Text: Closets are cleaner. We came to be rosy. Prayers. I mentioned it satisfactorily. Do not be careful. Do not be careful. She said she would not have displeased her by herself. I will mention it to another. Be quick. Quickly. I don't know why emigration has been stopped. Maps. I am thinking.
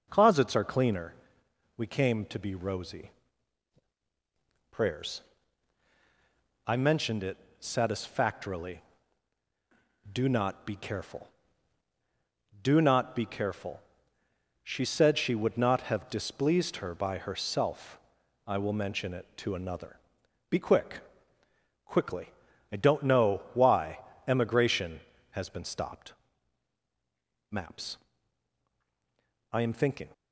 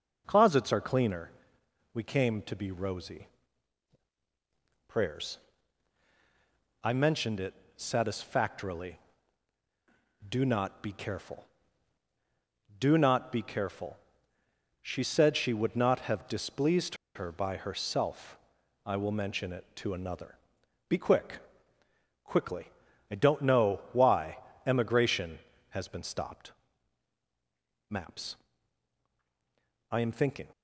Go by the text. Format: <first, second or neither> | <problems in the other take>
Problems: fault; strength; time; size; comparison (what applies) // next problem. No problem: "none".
first | pauses between "it" and "satisfactorily"; slight; at 7.5 s; 0.22 s long; slight in the first // pauses between "displeased" and "her"; slight; at 16.9 s; 0.19 s long // pauses between "why" and "emigration"; slight; at 24.3 s; 0.28 s long; slight in the first